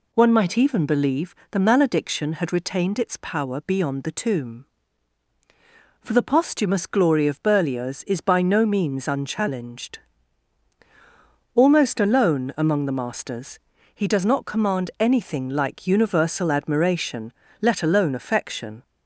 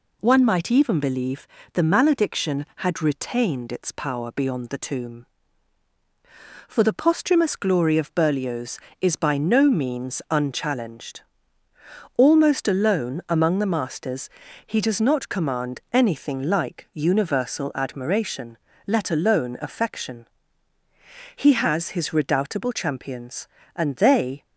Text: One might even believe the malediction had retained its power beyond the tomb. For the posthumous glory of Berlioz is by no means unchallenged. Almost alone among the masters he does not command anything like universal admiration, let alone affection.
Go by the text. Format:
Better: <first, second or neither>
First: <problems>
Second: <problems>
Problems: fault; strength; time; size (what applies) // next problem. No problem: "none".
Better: first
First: pauses between "believe" and "the"; slight; at 1.3 s; 0.18 s long // pauses between "masters" and "he"; slight; at 13.5 s; 0.36 s long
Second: pauses between "believe" and "the"; slight; at 1.4 s; 0.26 s long // pauses between "masters" and "he"; at 14.2 s; 0.38 s long // goes on to say "He has his redoubtable champions and they"; strong; from 21.3 s on; 3.0 s long